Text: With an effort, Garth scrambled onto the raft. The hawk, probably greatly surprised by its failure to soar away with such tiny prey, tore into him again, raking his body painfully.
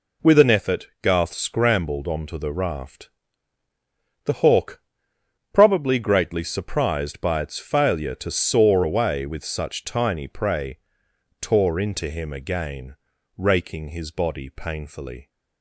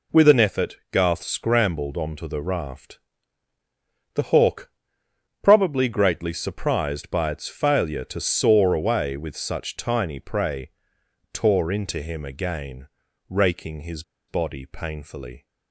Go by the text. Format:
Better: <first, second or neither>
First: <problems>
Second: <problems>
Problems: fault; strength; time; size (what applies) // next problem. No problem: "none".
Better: first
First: none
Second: pauses between "his" and "body"; slight; at 14.0 s; 0.27 s long